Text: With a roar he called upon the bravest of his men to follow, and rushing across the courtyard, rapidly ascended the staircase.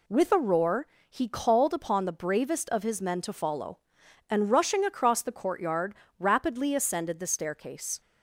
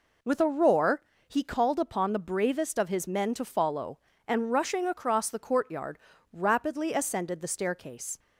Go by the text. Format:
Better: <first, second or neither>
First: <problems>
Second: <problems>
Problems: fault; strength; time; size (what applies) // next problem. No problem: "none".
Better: neither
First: pauses between "roar" and "he"; slight; at 0.8 s; 0.24 s long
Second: pauses between "roar" and "he"; slight; at 1.0 s; 0.26 s long